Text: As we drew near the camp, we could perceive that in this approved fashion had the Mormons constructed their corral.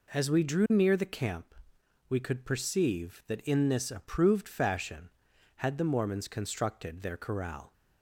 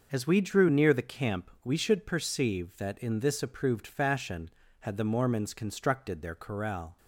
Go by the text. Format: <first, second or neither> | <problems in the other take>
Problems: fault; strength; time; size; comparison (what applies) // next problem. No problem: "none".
first | starts louder than the rest; noticeable; until 1.1 s; 6 dB // says "should" for "could"; at 1.7 s